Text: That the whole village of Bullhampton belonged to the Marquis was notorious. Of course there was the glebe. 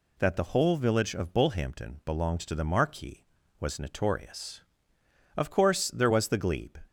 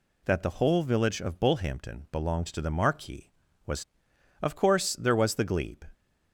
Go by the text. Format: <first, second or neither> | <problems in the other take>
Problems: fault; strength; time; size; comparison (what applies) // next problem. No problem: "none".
first | skips "notorious"; at 4.1 s